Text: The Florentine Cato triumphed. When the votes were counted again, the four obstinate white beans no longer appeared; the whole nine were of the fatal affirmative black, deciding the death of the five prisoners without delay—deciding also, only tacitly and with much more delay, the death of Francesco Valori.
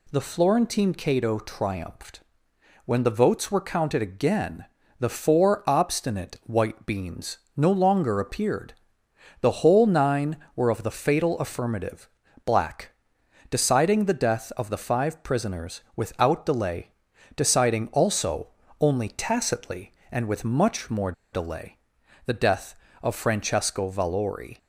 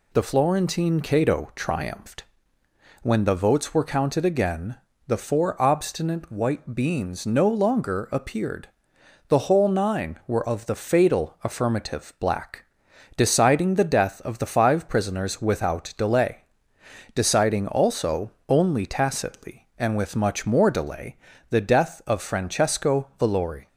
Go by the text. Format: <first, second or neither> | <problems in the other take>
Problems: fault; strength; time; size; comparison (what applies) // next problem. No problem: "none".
second | pauses between "beans" and "no"; slight; at 7.3 s; 0.18 s long // pauses between "affirmative" and "black"; at 12.0 s; 0.38 s long // pauses between "more" and "delay"; slight; at 21.1 s; 0.21 s long